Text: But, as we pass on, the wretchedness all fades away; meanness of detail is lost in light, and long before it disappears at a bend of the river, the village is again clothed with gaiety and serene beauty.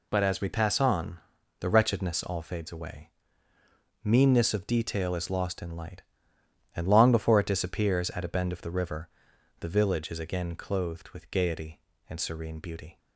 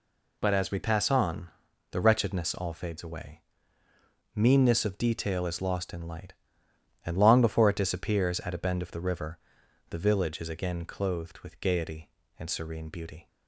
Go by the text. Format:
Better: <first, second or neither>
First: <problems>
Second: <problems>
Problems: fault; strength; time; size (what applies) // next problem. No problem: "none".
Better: neither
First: none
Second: none